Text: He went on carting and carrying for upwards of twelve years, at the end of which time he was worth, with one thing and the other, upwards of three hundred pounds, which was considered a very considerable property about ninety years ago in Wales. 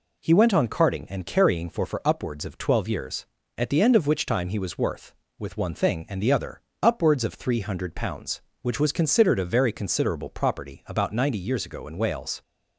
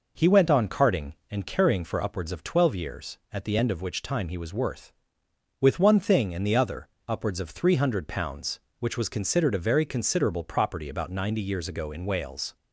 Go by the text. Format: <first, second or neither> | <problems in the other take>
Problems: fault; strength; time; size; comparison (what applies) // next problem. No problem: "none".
second | says "for" twice; at 1.8 s